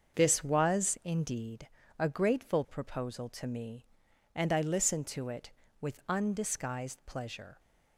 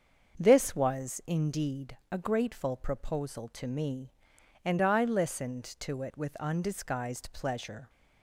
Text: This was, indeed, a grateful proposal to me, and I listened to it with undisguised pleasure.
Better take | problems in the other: neither | starts louder than the rest; the same in both

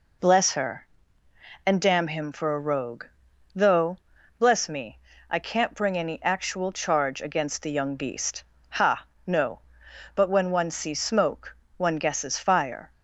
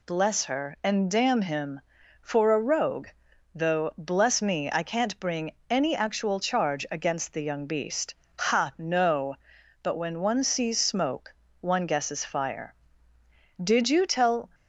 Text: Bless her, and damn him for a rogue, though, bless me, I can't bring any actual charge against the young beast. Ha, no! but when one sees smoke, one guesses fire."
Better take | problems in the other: first | pauses between "bring" and "any"; slight; at 5.5 s; 0.18 s long // goes on to say "Did you tell"; noticeable; from 13.6 s on; 0.88 s long

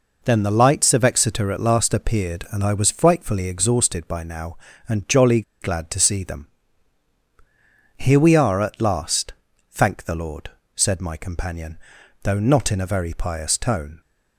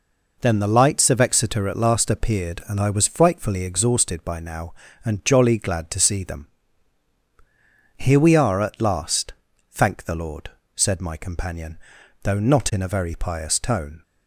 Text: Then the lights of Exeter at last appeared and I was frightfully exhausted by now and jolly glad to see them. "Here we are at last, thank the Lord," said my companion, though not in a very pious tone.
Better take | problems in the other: second | pauses between "jolly" and "glad"; slight; at 5.4 s; 0.19 s long

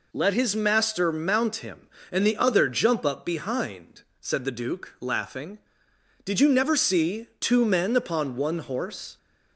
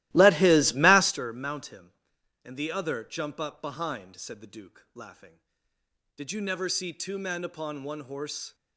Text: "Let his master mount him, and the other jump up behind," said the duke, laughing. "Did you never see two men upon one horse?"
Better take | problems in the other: first | starts louder than the rest; strong; until 1.2 s; 16 dB

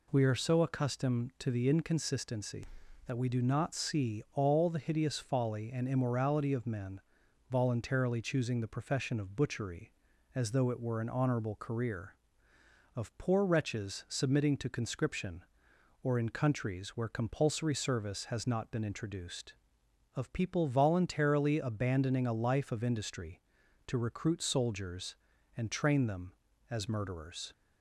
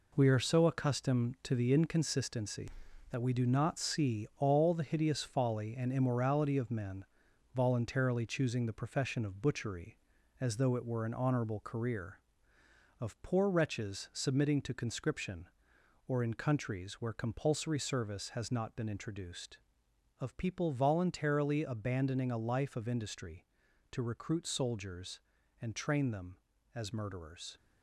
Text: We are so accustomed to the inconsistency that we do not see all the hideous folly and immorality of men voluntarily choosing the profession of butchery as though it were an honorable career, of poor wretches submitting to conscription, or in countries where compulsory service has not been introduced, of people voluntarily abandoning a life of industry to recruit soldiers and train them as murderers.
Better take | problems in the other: first | gets quieter; strong; throughout; 7.5 dB // pauses between "men" and "voluntarily"; noticeable; at 7.0 s; 0.50 s long; noticeable in the first

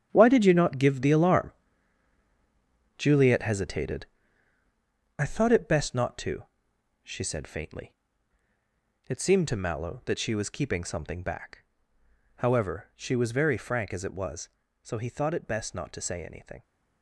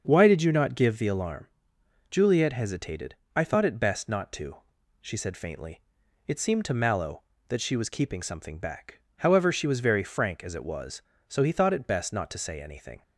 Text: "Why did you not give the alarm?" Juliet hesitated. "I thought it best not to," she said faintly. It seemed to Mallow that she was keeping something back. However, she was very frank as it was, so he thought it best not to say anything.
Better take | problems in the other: second | gets quieter; strong; throughout; 11.5 dB // starts louder than the rest; strong; until 1.1 s; 9.5 dB; also in the second

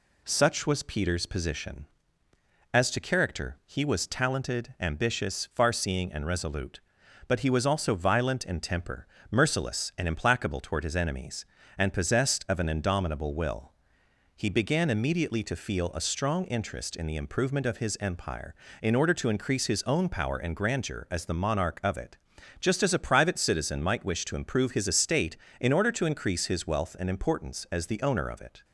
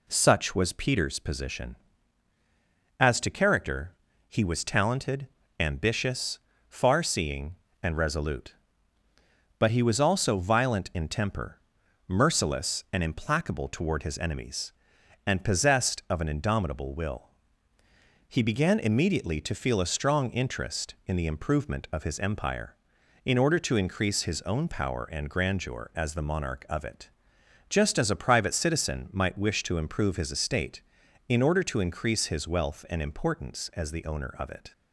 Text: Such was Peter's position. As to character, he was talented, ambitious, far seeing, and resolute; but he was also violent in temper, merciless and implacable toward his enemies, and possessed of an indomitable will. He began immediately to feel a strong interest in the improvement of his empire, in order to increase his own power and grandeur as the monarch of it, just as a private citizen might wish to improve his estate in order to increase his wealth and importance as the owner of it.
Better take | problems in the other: neither | none

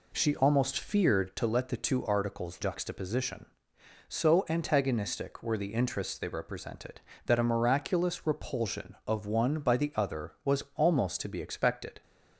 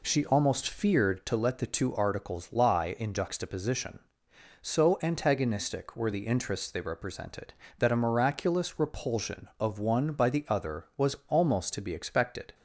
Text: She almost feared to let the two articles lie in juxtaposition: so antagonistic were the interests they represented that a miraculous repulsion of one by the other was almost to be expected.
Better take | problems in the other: second | skips "lie in"; at 2.5 s

